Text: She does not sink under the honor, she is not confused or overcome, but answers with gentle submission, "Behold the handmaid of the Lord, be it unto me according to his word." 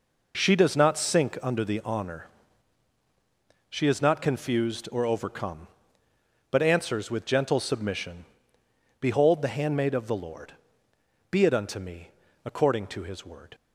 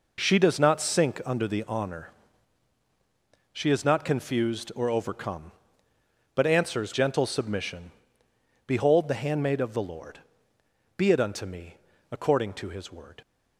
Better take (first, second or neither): first